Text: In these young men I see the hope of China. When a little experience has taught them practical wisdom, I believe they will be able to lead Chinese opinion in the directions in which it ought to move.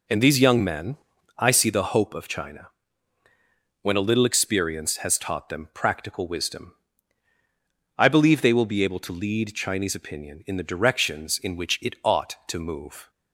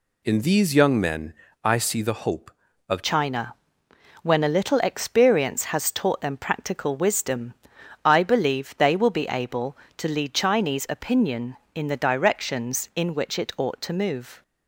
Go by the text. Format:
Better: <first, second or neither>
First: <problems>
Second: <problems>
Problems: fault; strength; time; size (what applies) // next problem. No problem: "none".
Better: first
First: pauses between "men" and "I"; at 0.9 s; 0.40 s long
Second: pauses between "men" and "I"; slight; at 1.3 s; 0.32 s long // changes voice at "China"; from 3.0 s on; 11.4 s long